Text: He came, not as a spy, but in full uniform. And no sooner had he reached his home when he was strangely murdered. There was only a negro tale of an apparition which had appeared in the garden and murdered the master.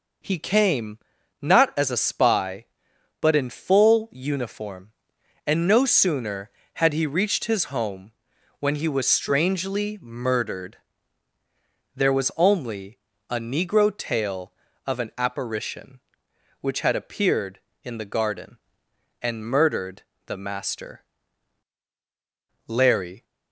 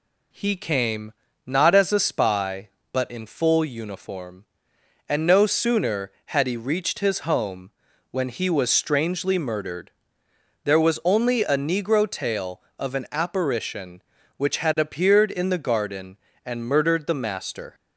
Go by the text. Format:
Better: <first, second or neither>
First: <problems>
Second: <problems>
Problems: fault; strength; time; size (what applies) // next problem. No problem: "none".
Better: second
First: pauses between "home" and "when"; noticeable; at 8.1 s; 0.48 s long // pauses between "only" and "a"; slight; at 12.9 s; 0.30 s long // pauses between "murdered" and "the"; slight; at 20.0 s; 0.24 s long // goes on to say "Larry"; from 22.6 s on; 0.56 s long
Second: pauses between "home" and "when"; at 7.6 s; 0.42 s long